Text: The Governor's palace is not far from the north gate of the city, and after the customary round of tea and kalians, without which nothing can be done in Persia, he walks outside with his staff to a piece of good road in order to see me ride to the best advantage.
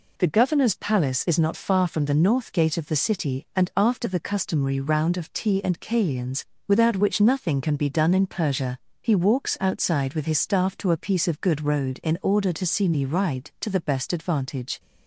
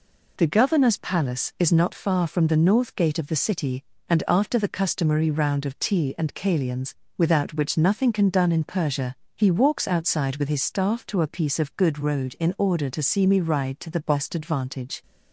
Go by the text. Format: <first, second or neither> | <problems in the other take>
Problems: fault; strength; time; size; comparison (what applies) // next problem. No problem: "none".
first | skips "be"; at 8.2 s